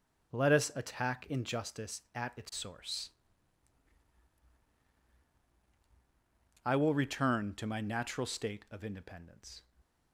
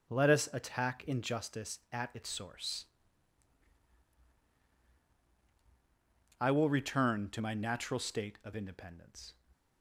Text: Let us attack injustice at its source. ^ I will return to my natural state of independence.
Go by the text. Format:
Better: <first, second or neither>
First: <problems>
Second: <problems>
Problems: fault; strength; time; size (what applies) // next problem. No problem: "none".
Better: neither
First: starts louder than the rest; until 1.4 s; 6.5 dB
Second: starts louder than the rest; until 1.1 s; 6 dB